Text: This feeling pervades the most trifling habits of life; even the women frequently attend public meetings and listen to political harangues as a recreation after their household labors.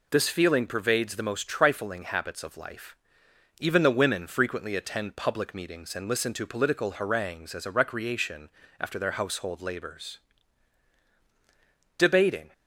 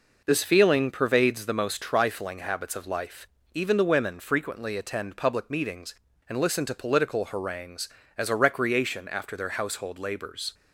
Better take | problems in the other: second | pauses between "recreation" and "after"; slight; at 8.4 s; 0.30 s long // goes on to say "Debating"; from 11.9 s on; 0.54 s long

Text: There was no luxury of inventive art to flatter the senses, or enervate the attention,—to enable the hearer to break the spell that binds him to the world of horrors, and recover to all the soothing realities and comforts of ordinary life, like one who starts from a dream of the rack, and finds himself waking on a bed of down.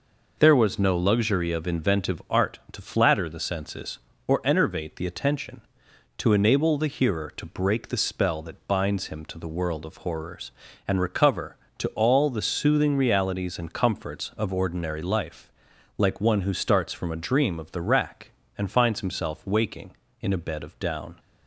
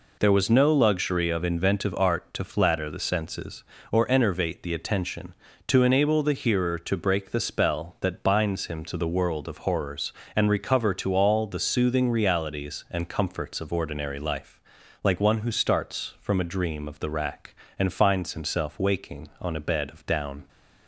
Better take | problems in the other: second | says "in" for "on"; at 20.2 s

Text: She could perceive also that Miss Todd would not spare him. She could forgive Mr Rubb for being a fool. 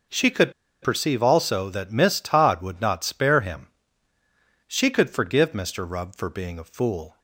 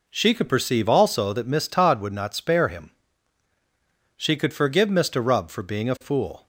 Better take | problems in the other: second | pauses between "could" and "perceive"; slight; at 0.5 s; 0.32 s long

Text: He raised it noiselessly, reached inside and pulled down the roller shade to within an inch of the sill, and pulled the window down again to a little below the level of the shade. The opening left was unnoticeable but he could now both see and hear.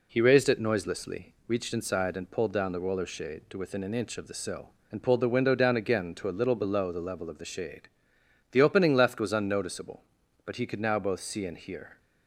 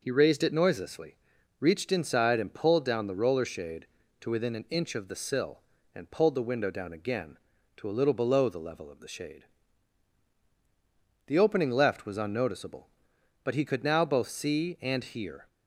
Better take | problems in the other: neither | none

